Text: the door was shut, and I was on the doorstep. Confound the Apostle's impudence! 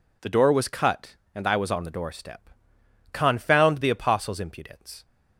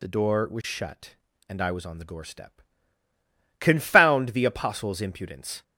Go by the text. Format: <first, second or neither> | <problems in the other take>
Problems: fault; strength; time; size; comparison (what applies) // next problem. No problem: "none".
second | says "cut" for "shut"; at 0.6 s